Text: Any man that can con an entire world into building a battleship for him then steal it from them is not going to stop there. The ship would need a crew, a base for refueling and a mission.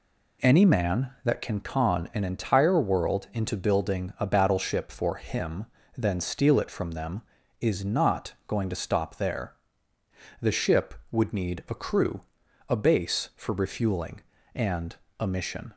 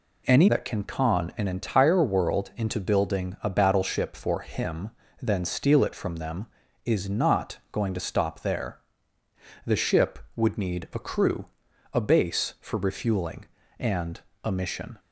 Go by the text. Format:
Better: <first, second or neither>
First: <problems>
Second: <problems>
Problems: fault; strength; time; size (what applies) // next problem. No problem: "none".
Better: first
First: pauses between "him" and "then"; slight; at 5.6 s; 0.30 s long // pauses between "and" and "a"; slight; at 14.9 s; 0.24 s long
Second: skips "man"; at 0.4 s // pauses between "him" and "then"; slight; at 4.9 s; 0.30 s long // pauses between "and" and "a"; slight; at 14.1 s; 0.24 s long